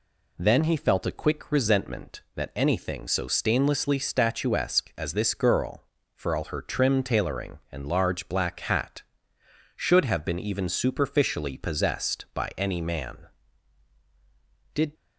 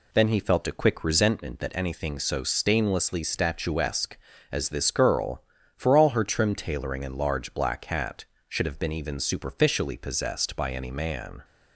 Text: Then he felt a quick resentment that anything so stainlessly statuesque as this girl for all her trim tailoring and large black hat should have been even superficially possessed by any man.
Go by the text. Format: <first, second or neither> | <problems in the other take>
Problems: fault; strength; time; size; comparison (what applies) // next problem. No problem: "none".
second | goes on to say "Did"; slight; from 14.7 s on; 0.20 s long